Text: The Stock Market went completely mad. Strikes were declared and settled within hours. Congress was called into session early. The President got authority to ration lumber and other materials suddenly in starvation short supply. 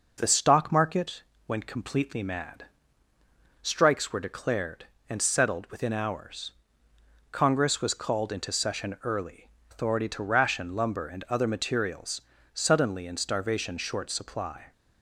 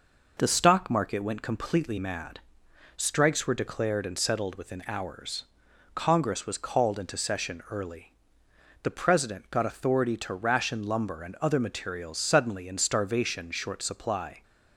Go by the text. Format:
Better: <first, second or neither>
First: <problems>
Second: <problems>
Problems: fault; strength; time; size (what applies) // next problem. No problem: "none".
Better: second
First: pauses between "Market" and "went"; slight; at 1.2 s; 0.24 s long // skips "The President got"; at 9.5 s // pauses between "materials" and "suddenly"; slight; at 12.2 s; 0.30 s long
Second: none